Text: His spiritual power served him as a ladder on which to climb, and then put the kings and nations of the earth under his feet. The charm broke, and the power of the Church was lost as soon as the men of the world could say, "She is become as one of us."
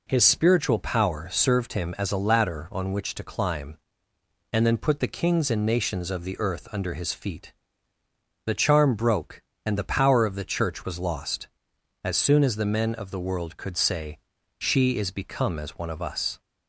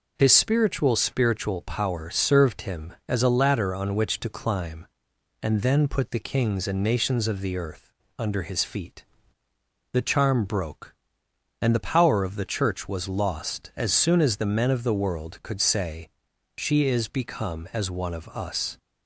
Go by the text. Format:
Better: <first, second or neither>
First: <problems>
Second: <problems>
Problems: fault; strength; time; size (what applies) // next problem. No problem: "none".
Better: first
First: none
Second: says "spiritual" twice; at 0.9 s // pauses between "earth" and "under"; slight; at 7.9 s; 0.26 s long